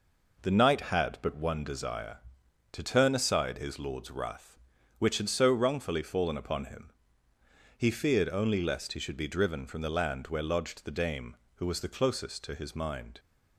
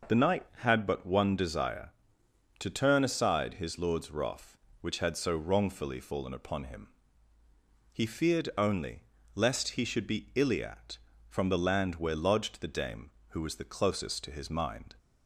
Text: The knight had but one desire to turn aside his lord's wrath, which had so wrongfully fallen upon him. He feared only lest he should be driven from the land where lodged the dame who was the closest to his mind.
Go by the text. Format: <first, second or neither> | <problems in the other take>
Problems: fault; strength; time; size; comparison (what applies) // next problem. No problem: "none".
first | pauses between "only" and "lest"; slight; at 9.0 s; 0.32 s long // says "iliat" for "driven"; at 10.3 s